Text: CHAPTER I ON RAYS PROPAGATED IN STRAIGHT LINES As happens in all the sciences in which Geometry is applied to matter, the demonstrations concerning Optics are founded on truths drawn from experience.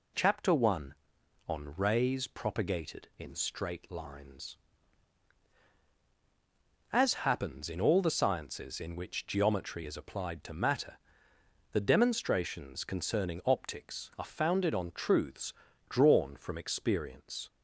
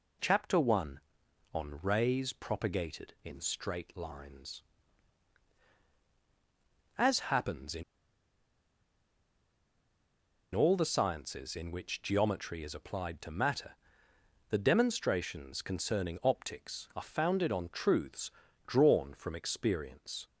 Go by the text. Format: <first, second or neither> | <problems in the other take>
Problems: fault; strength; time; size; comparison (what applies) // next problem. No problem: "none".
first | pauses between "in" and "all"; strong; at 7.8 s; 2.7 s long // pauses between "truths" and "drawn"; slight; at 18.3 s; 0.36 s long; slight in the first